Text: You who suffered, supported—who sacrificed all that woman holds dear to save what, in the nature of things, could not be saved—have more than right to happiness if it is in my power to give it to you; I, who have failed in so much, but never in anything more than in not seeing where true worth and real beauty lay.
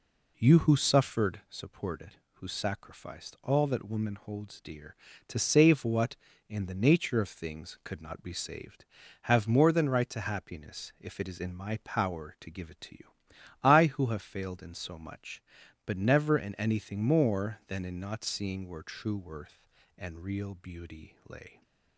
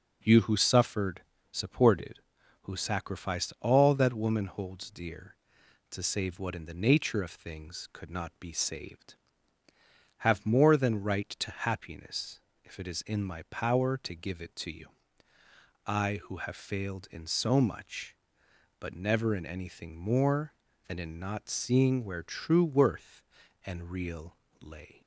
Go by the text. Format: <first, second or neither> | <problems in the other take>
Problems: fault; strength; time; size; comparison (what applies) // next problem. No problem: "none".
first | pauses between "happiness" and "if"; slight; at 12.3 s; 0.24 s long // skips "beauty"; at 24.4 s